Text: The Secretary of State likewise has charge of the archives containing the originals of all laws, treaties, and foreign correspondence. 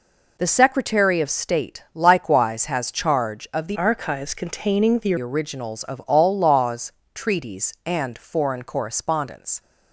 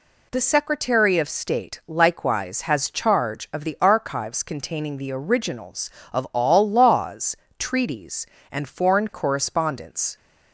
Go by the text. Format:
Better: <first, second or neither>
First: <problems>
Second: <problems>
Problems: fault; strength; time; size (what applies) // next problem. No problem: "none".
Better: second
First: changes voice from "archives" to "the"; from 3.7 to 5.1 s; 1.4 s long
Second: none